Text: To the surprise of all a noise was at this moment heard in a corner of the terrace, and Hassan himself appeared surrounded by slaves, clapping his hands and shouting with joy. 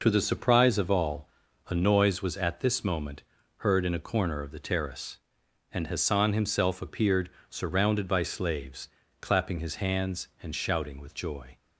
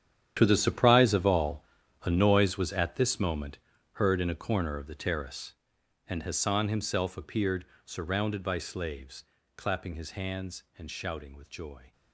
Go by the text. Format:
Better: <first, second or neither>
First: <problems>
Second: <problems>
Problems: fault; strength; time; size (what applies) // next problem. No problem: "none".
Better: first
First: pauses between "all" and "a"; at 1.2 s; 0.40 s long // pauses between "moment" and "heard"; slight; at 3.2 s; 0.36 s long // pauses between "appeared" and "surrounded"; slight; at 7.3 s; 0.20 s long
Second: gets quieter; strong; throughout; 15 dB // pauses between "all" and "a"; at 1.6 s; 0.40 s long // pauses between "moment" and "heard"; slight; at 3.5 s; 0.36 s long // pauses between "appeared" and "surrounded"; slight; at 7.6 s; 0.20 s long